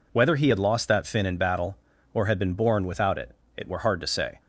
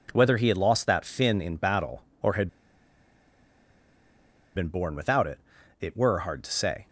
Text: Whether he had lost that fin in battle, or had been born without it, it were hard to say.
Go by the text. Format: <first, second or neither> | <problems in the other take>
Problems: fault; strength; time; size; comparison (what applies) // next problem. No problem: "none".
first | pauses between "had" and "been"; strong; at 2.4 s; 2.0 s long